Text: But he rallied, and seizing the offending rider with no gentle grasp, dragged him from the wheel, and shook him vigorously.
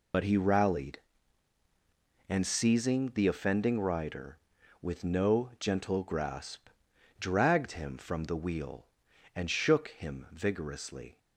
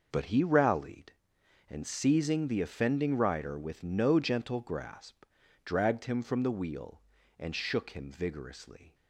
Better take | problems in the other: second | loses the start of "But"; at 0.1 s; 65 ms

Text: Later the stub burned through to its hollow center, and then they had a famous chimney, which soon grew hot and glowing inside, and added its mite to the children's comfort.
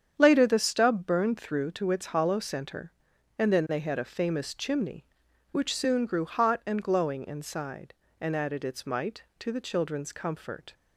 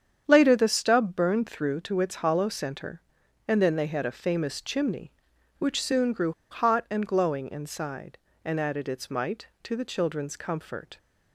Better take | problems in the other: first | starts louder than the rest; strong; until 1.2 s; 8 dB; strong in the first // pauses between "grew" and "hot"; slight; at 6.3 s; 0.20 s long

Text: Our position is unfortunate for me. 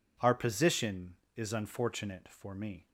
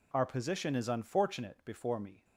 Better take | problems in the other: first | says "before" for "for"; at 1.6 s

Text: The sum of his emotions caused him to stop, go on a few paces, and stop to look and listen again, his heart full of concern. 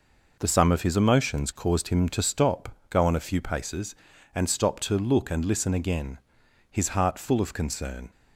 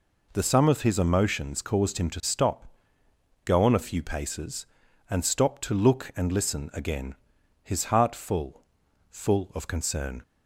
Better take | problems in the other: first | says "full" twice; at 9.0 s

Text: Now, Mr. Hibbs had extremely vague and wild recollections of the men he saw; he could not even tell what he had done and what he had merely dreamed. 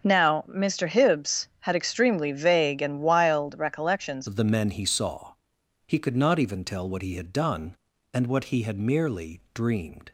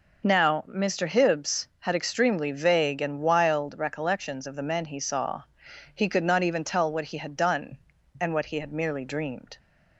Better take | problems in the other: second | starts louder than the rest; until 1.0 s; 6.5 dB // changes voice at "of"; from 4.2 s on; 5.9 s long

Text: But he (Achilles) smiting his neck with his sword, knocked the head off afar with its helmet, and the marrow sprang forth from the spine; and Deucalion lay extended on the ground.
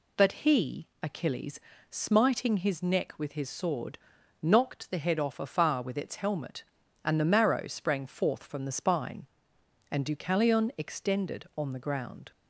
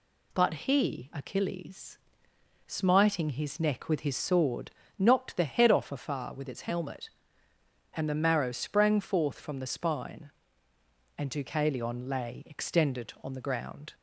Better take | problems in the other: second | skips "lay"; at 10.7 s

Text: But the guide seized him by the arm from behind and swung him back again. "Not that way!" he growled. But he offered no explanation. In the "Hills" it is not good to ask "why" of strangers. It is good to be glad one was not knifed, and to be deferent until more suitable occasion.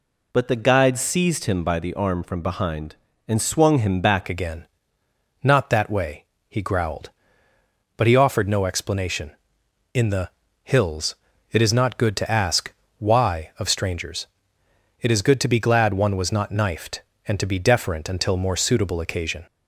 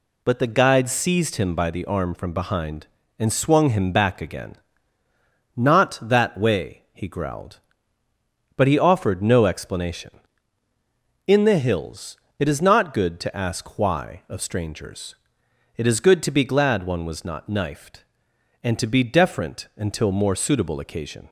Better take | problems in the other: second | changes voice at "again"; from 4.2 s on; 15.2 s long // pauses between "the" and "Hills"; slight; at 10.2 s; 0.34 s long // pauses between "Hills" and "it"; slight; at 11.1 s; 0.36 s long; slight in the second // pauses between "ask" and "why"; slight; at 12.7 s; 0.26 s long

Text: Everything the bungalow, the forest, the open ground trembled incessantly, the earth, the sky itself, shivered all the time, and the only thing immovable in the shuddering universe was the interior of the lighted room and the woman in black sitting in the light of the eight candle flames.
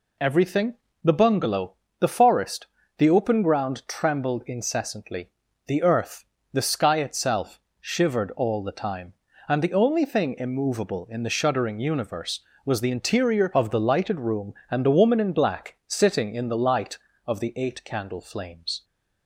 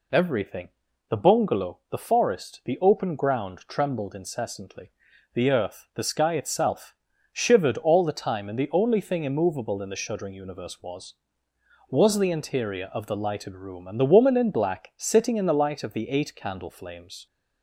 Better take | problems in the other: first | pauses between "Everything" and "the"; at 0.6 s; 0.40 s long; slight in the first // says "was" twice; at 11.8 s

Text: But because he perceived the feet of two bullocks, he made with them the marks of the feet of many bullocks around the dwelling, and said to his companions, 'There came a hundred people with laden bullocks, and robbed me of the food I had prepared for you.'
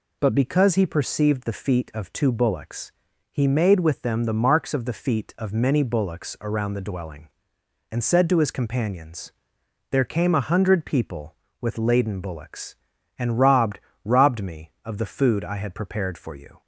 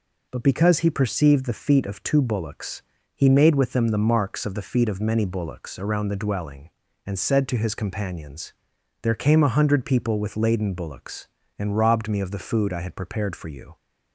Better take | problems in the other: second | says "robbed" twice; at 14.0 s

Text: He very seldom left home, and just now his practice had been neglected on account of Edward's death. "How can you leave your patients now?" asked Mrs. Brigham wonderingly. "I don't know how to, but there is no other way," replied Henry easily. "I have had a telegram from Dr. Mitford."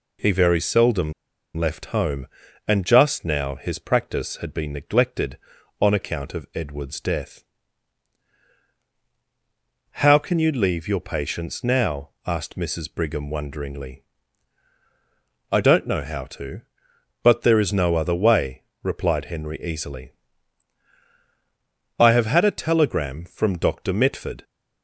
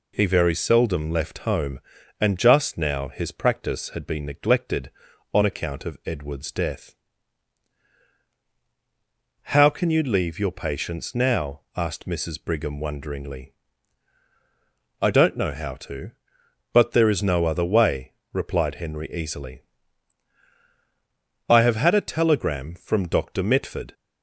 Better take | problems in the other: second | pauses between "seldom" and "left"; at 1.1 s; 0.44 s long

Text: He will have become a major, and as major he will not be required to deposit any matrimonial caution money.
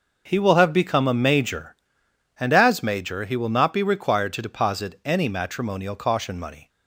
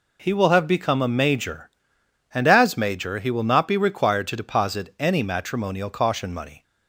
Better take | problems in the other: second | starts louder than the rest; noticeable; until 1.8 s; 6 dB

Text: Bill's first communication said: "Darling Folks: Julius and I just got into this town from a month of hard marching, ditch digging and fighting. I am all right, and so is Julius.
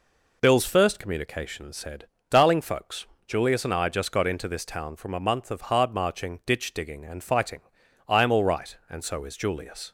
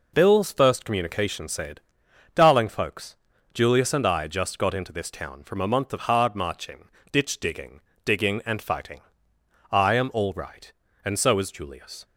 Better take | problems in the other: first | says "digging" twice; at 8.0 s

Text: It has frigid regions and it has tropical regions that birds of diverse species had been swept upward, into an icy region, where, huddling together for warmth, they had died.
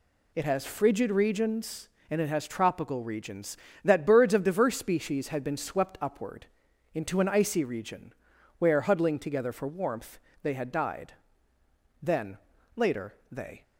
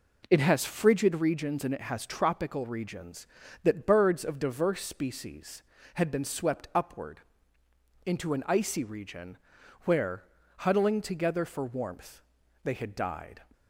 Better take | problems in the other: second | goes on to say "Then later they"; from 12.0 s on; 1.6 s long

